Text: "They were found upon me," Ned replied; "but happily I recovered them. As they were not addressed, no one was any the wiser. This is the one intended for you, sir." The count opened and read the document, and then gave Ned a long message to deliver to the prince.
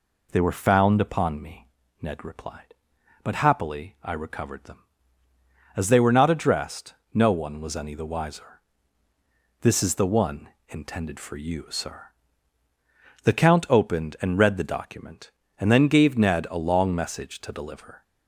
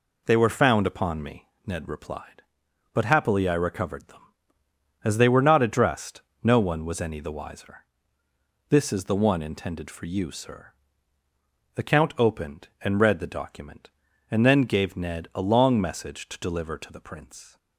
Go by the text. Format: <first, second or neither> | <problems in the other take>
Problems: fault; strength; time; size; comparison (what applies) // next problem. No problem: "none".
second | pauses between "one" and "intended"; slight; at 10.4 s; 0.20 s long // stops before "to the prince"; at 18.0 s